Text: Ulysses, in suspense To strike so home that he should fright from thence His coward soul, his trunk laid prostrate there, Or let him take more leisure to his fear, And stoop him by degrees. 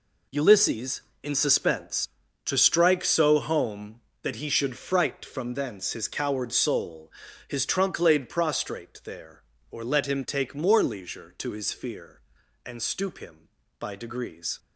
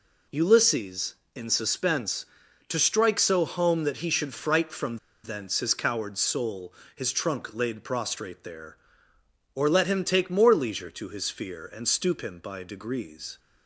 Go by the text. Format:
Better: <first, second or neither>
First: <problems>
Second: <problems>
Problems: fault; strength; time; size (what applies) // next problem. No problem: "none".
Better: first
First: none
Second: pauses between "from" and "thence"; slight; at 4.9 s; 0.26 s long